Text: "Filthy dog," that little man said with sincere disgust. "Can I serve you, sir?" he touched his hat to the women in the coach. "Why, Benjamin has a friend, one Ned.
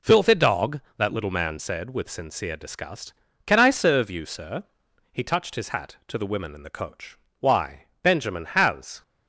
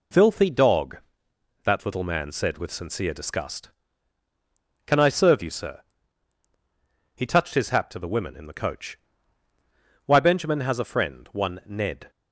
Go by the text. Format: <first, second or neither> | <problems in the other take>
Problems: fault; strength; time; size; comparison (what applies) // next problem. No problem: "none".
second | stops before "a friend one Ned"; at 9.0 s